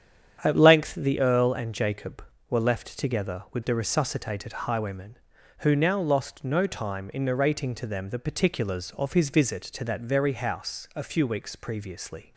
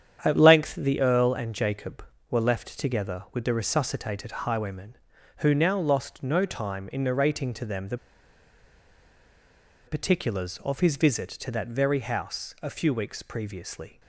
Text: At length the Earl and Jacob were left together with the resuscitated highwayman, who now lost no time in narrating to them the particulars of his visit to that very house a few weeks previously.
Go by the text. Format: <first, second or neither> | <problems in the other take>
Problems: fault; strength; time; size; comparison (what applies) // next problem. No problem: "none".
first | starts louder than the rest; strong; until 1.2 s; 9 dB; strong in the first // pauses between "the" and "particulars"; strong; at 7.9 s; 1.9 s long